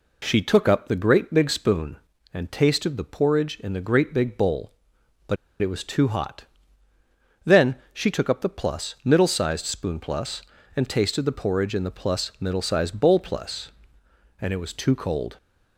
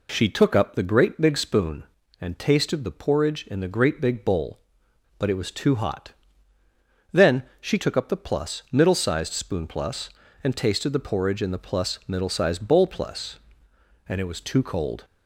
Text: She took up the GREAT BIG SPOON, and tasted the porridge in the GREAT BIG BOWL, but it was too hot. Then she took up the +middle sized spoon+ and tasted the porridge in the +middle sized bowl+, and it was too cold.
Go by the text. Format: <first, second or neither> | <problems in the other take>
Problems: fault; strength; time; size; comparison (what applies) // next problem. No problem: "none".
second | pauses between "but" and "it"; slight; at 5.3 s; 0.24 s long // pauses between "Then" and "she"; slight; at 7.7 s; 0.18 s long; slight in the second